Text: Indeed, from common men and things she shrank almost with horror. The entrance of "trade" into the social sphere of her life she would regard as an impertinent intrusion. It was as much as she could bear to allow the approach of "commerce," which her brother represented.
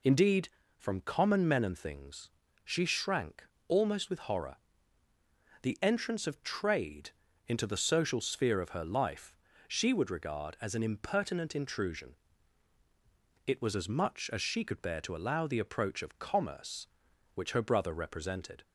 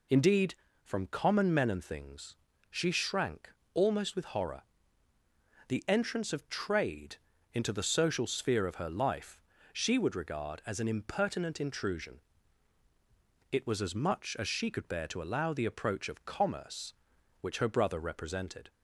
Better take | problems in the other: neither | pauses between "things" and "she"; slight; the same in both // pauses between "shrank" and "almost"; slight; the same in both // pauses between "trade" and "into"; the same in both // pauses between "life" and "she"; slight; the same in both

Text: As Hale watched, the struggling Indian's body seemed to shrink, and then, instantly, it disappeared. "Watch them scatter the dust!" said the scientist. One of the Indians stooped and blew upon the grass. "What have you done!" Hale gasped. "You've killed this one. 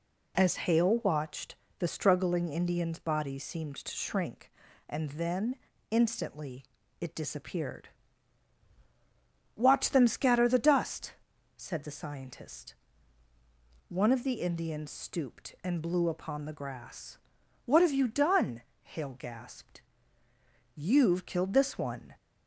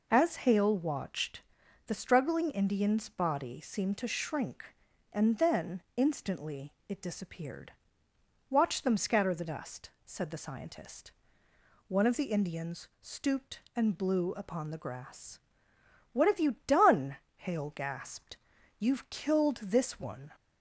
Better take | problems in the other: neither | none

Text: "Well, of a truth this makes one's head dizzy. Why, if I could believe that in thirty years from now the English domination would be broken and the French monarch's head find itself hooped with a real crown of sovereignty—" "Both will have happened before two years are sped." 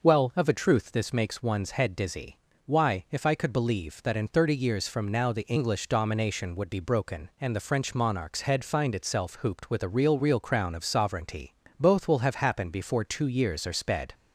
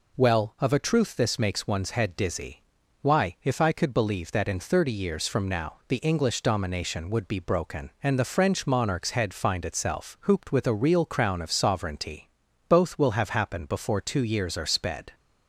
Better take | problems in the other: second | says "real" twice; at 10.1 s

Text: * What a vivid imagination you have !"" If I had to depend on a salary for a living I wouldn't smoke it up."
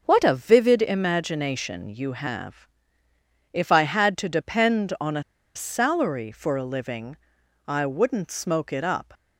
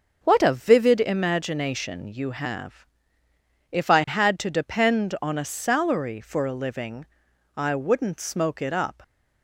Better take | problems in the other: second | pauses between "a" and "salary"; slight; at 5.2 s; 0.32 s long // pauses between "living" and "I"; noticeable; at 7.1 s; 0.50 s long; noticeable in the second

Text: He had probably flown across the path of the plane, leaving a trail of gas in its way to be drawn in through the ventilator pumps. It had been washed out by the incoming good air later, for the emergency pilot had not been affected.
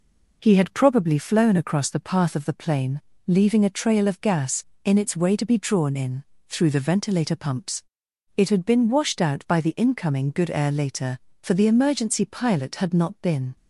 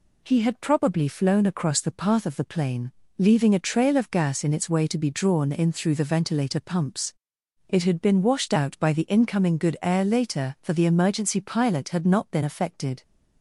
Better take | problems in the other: second | pauses between "in" and "through"; slight; at 6.2 s; 0.24 s long // stops before "affected"; at 13.5 s

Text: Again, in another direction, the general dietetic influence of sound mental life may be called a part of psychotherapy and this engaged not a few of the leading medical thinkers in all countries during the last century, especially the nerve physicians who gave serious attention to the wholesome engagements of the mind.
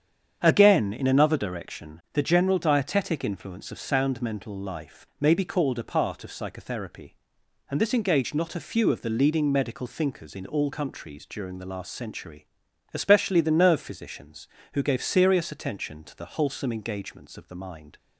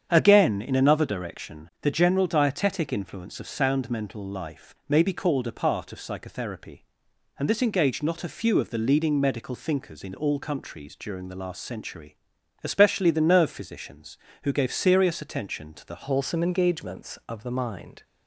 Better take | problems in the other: first | starts louder than the rest; strong; until 1.1 s; 8.5 dB; strong in the first // changes voice at "wholesome"; from 16.0 s on; 2.0 s long

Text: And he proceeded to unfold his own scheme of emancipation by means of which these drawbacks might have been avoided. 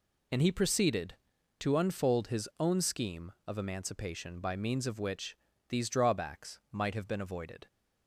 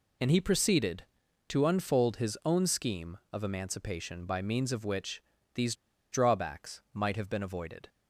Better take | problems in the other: first | pauses between "which" and "these"; slight; at 5.2 s; 0.34 s long; slight in the first // pauses between "these" and "drawbacks"; at 5.7 s; 0.37 s long

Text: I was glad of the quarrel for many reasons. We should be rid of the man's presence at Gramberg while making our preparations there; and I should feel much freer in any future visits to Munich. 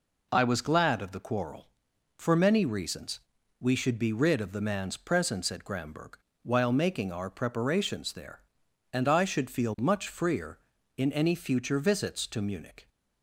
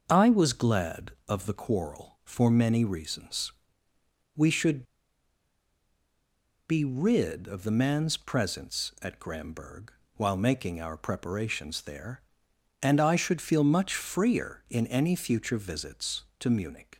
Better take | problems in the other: first | starts louder than the rest; until 1.0 s; 6.5 dB // pauses between "should" and "be"; strong; at 4.8 s; 1.8 s long // pauses between "Gramberg" and "while"; slight; at 9.8 s; 0.28 s long; slight in the first

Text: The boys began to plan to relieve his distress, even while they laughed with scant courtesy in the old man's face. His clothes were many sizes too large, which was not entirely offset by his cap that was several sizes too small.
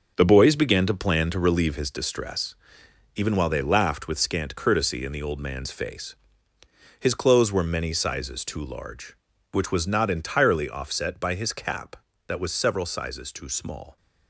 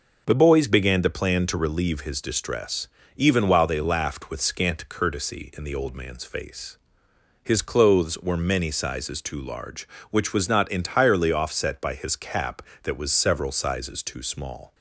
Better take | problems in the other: second | gets quieter; strong; throughout; 8.5 dB

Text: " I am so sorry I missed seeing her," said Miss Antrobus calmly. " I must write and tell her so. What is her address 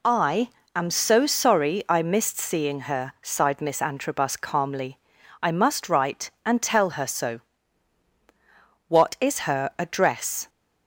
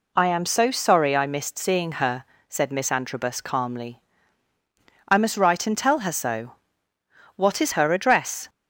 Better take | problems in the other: second | pauses between "I" and "am"; slight; at 0.4 s; 0.26 s long // says "sighed" for "said"; at 3.2 s

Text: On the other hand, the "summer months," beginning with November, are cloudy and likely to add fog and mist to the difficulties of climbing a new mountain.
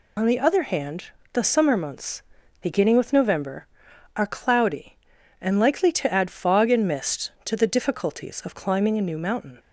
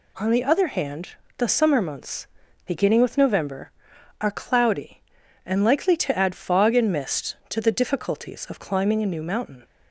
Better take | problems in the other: second | loses the start of "On"; at 0.1 s; 55 ms

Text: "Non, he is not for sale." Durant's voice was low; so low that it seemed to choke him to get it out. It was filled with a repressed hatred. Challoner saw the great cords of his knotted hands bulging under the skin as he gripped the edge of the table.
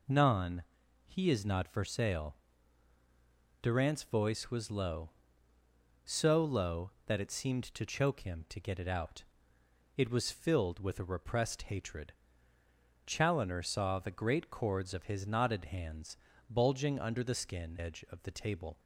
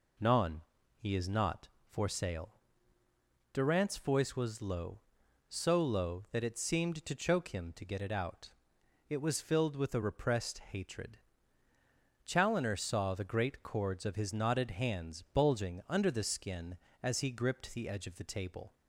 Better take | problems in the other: second | pauses between "hands" and "bulging"; slight; at 16.1 s; 0.32 s long // skips "as he gripped the"; at 17.7 s

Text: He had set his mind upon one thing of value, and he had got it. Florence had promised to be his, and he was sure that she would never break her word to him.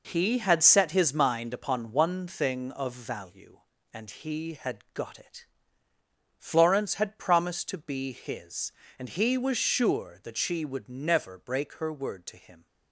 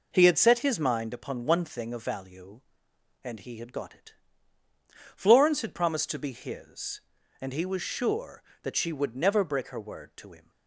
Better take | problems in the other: second | gets quieter; strong; throughout; 7.5 dB

